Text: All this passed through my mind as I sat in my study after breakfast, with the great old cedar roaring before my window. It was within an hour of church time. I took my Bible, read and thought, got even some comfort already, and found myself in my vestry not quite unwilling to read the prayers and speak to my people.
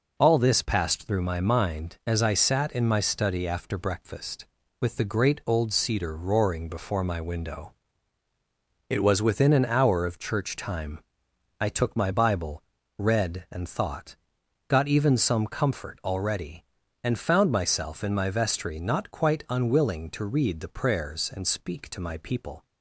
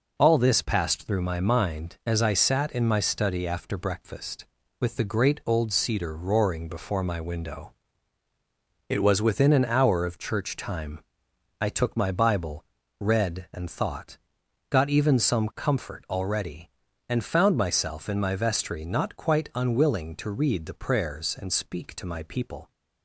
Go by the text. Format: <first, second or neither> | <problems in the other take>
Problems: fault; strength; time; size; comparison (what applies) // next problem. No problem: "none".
neither | none